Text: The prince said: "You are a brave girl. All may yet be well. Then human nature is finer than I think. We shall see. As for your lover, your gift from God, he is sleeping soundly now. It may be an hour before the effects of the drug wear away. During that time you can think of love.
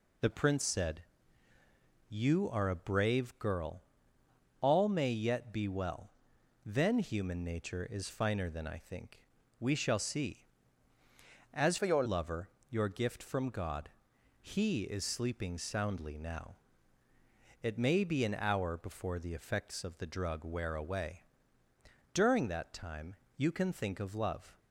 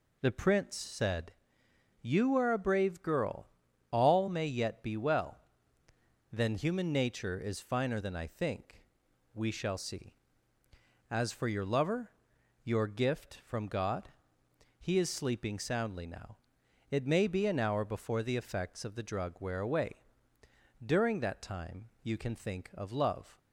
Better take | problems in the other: second | changes voice from "for" to "your"; from 11.7 to 12.0 s; 0.3 s long // pauses between "time" and "you"; slight; at 23.1 s; 0.24 s long

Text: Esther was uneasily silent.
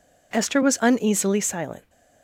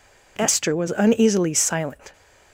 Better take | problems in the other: neither | none

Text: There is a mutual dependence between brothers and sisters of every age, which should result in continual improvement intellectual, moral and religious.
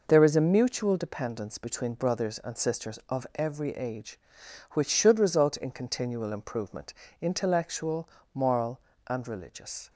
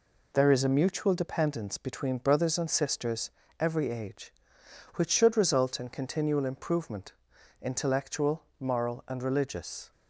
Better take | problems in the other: first | skips "of"; at 3.4 s // pauses between "improvement" and "intellectual"; noticeable; at 7.1 s; 0.48 s long; slight in the first

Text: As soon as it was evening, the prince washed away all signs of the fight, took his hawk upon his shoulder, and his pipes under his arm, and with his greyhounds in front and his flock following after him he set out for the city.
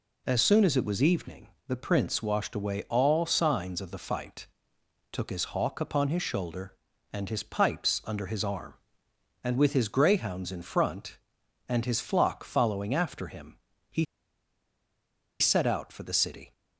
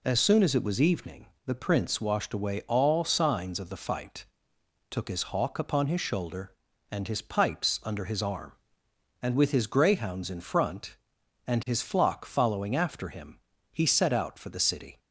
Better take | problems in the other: second | pauses between "him" and "he"; slight; at 13.5 s; 0.32 s long; slight in the second // pauses between "he" and "set"; strong; at 14.0 s; 1.3 s long

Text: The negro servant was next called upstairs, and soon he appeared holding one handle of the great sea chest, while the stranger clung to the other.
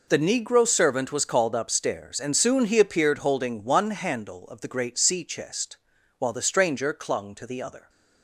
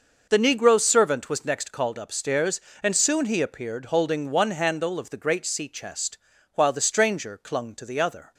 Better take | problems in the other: second | skips "next"; at 1.2 s

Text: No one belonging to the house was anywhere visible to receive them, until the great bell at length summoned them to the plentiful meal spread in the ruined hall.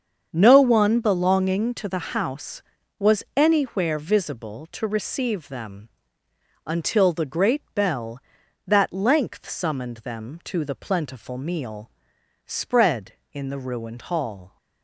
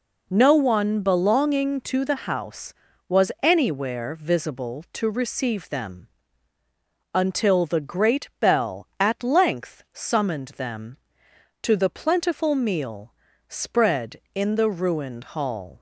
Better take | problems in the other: second | starts louder than the rest; strong; until 1.3 s; 7 dB // says "that" for "at"; at 8.6 s // pauses between "meal" and "spread"; noticeable; at 11.9 s; 0.54 s long; slight in the second

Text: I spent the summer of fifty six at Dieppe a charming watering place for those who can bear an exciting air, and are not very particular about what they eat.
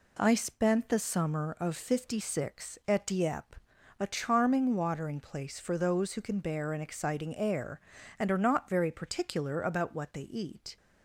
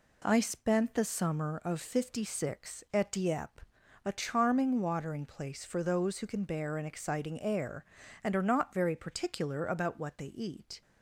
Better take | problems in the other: neither | pauses between "Dieppe" and "a"; the same in both

